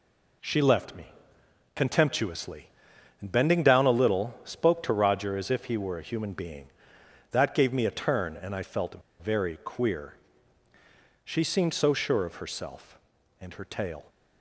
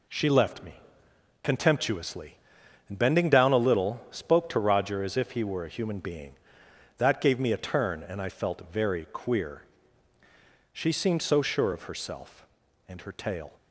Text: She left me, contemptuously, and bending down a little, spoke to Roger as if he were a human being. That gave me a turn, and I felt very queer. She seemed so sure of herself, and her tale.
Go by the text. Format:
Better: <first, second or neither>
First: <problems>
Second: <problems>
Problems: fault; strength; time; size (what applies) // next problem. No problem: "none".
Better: second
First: pauses between "felt" and "very"; slight; at 9.0 s; 0.21 s long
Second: none